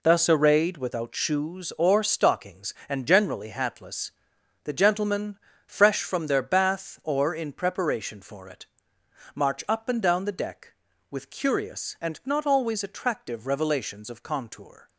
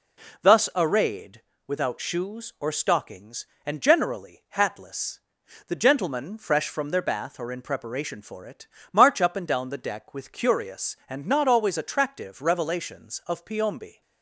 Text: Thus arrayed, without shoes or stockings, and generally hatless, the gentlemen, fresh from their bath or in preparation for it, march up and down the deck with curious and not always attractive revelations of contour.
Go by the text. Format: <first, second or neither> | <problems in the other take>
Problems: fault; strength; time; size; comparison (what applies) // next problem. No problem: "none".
first | says "piombi" for "contour"; at 13.4 s